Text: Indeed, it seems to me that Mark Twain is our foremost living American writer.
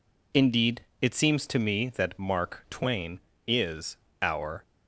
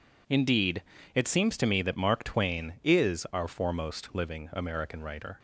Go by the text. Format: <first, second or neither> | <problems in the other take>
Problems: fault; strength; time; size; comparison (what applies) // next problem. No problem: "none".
second | pauses between "is" and "our"; slight; at 3.9 s; 0.24 s long // stops before "foremost living American writer"; at 4.6 s